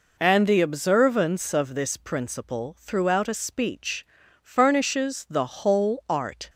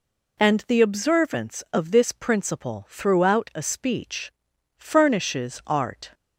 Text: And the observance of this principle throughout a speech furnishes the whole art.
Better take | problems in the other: first | pauses between "speech" and "furnishes"; noticeable; at 4.3 s; 0.46 s long; also in the first // skips "the whole"; at 5.6 s

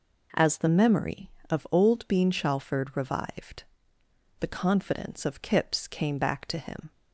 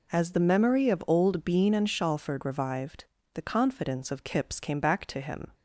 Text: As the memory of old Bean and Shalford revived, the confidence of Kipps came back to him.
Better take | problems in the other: second | skips "and"; at 2.2 s

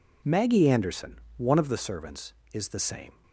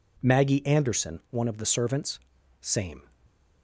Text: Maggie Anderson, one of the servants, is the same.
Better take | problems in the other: first | skips "is the"; at 2.3 s

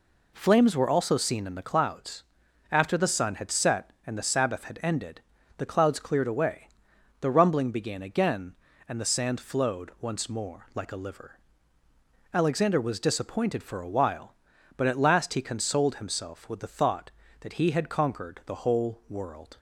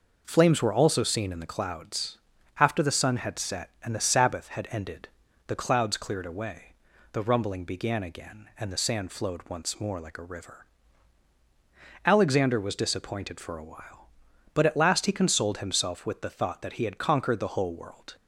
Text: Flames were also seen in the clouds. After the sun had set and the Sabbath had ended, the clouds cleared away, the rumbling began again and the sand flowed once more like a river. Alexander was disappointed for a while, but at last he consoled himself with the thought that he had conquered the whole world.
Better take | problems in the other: second | says "liver" for "river"; at 10.9 s

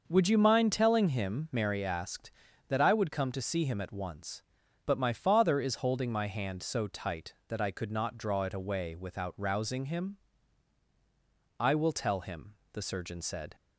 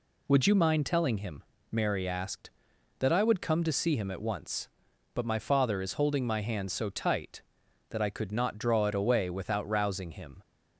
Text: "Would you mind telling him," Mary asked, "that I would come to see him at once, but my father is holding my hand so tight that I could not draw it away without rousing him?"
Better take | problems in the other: second | starts louder than the rest; until 1.0 s; 6 dB // goes on to say "I will tell him the surgeon said"; strong; from 11.5 s on; 1.9 s long

